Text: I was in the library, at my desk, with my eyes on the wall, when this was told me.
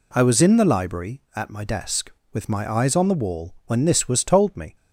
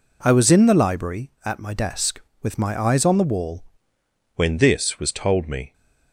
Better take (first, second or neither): first